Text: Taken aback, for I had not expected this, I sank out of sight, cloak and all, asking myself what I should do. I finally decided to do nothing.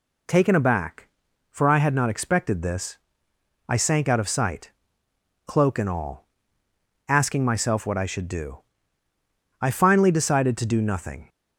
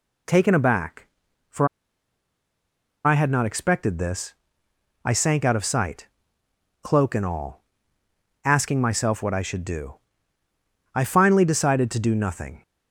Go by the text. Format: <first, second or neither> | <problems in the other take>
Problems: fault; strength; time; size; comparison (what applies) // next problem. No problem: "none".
first | pauses between "for" and "I"; strong; at 1.6 s; 1.3 s long